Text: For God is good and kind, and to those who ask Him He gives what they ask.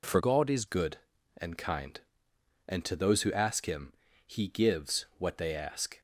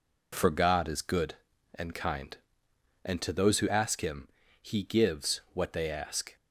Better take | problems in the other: second | changes voice from "God" to "is"; from 0.1 to 0.6 s; 0.5 s long // pauses between "Him" and "He"; slight; at 3.9 s; 0.32 s long; slight in the second

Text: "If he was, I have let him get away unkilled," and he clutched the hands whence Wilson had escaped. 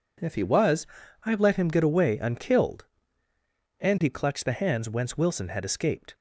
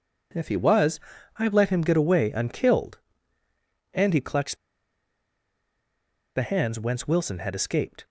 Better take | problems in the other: first | pauses between "clutched" and "the"; strong; at 4.5 s; 1.7 s long

